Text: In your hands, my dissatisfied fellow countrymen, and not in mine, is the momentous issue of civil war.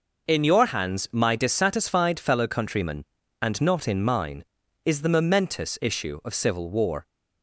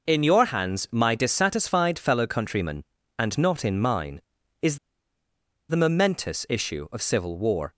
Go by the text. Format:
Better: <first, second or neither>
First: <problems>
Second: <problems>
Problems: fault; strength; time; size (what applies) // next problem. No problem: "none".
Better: first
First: none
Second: pauses between "is" and "the"; noticeable; at 4.7 s; 0.92 s long